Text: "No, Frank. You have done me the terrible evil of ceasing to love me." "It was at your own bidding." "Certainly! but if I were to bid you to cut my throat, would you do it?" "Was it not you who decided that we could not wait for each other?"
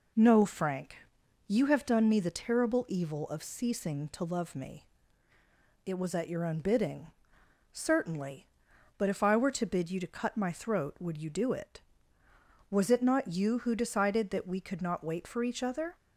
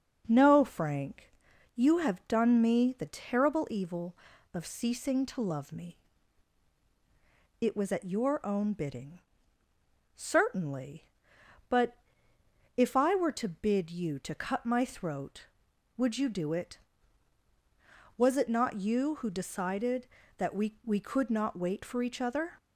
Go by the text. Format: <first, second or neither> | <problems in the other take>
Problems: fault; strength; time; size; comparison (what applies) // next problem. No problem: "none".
first | pauses between "but" and "if"; noticeable; at 11.9 s; 0.80 s long // says "we" twice; at 20.8 s